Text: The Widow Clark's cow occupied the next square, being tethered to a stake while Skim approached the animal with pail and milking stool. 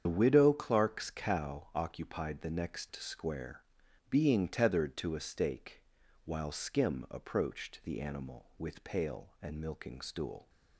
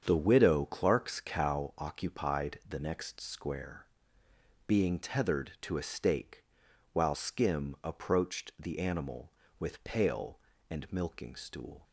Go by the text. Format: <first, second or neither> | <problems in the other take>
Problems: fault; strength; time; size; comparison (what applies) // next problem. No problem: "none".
second | loses the start of "The"; at 0.0 s; 70 ms // starts louder than the rest; strong; until 1.0 s; 8 dB; strong in the second // pauses between "stake" and "while"; at 5.8 s; 0.42 s long; noticeable in the second